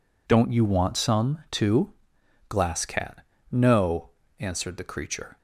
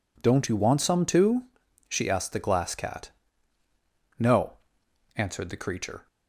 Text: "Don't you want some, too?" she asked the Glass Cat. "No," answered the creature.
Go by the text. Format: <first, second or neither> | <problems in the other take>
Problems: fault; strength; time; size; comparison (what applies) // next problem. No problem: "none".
second | skips "she asked the"; at 2.2 s